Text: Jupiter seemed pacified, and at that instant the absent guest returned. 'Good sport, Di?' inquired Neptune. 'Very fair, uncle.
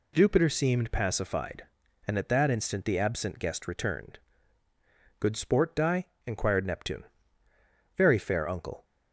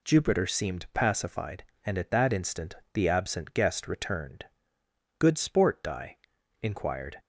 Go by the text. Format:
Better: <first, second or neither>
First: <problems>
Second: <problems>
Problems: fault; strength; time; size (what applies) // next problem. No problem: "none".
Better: first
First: none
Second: pauses between "instant" and "the"; slight; at 2.7 s; 0.20 s long // stops before "Neptune Very fair uncle"; at 7.1 s